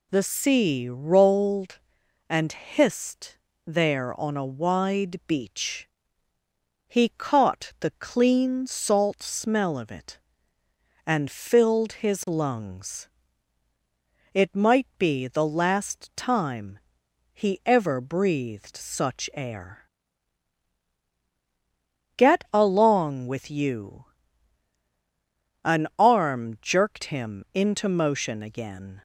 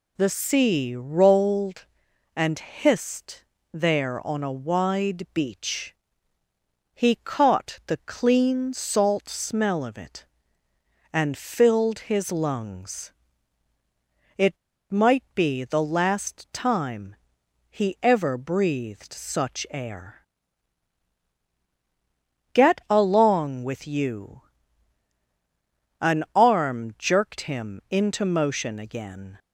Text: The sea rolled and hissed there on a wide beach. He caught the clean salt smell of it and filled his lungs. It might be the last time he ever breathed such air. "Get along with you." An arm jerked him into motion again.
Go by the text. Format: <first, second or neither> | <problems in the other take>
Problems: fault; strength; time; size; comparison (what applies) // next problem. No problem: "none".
first | pauses between "hissed" and "there"; slight; at 3.4 s; 0.30 s long; slight in the first // pauses between "It" and "might"; slight; at 14.5 s; 0.33 s long // pauses between "time" and "he"; noticeable; at 17.1 s; 0.56 s long; noticeable in the first